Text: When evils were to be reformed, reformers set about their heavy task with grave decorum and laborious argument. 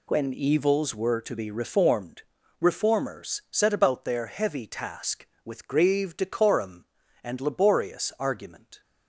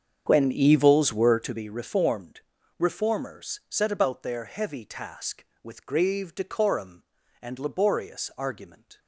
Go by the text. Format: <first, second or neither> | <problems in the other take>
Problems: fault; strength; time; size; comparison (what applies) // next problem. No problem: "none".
first | starts louder than the rest; strong; until 1.6 s; 7 dB